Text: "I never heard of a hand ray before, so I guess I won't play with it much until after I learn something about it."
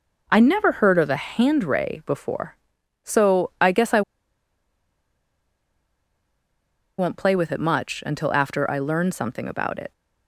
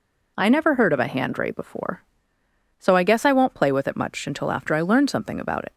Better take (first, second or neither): second